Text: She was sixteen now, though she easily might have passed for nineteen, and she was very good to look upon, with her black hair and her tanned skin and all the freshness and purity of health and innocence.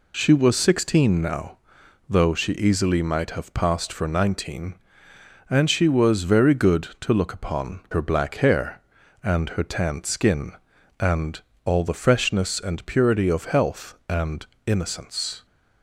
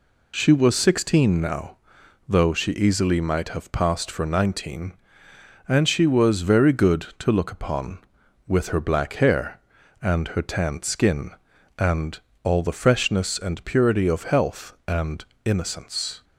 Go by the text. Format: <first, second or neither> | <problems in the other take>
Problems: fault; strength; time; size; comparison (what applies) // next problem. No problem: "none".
second | skips "with"; at 7.8 s // pauses between "and" and "all"; slight; at 11.3 s; 0.24 s long; slight in the second // pauses between "and" and "innocence"; slight; at 14.4 s; 0.20 s long; slight in the second